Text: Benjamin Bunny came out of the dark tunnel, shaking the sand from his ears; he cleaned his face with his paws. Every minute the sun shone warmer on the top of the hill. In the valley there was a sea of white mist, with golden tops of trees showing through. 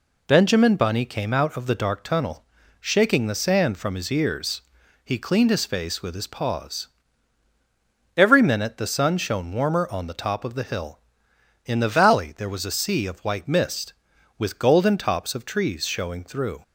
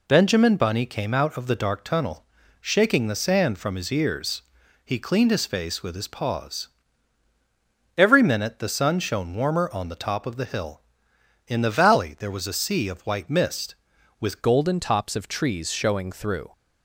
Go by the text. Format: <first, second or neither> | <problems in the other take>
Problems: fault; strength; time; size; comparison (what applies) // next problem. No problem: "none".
first | changes voice at "golden"; from 14.4 s on; 2.1 s long